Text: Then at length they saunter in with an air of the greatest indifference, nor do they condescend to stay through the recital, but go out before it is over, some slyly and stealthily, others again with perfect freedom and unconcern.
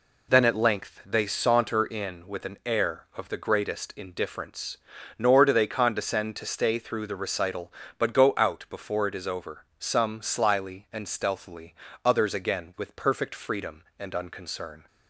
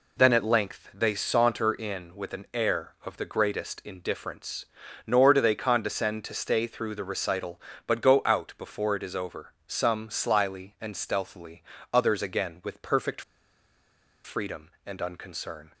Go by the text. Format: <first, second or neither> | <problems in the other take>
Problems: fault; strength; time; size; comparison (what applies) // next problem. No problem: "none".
first | pauses between "perfect" and "freedom"; at 13.2 s; 1.0 s long